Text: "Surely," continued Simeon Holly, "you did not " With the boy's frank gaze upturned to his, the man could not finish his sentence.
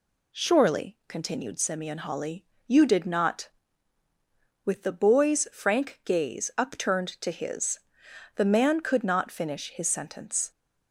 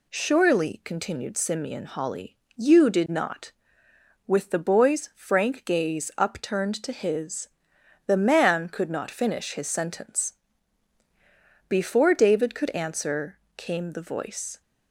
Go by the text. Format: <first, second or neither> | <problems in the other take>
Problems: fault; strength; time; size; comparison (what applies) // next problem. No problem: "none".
first | goes on to say "Before David could answer came the voice"; strong; from 11.6 s on; 2.9 s long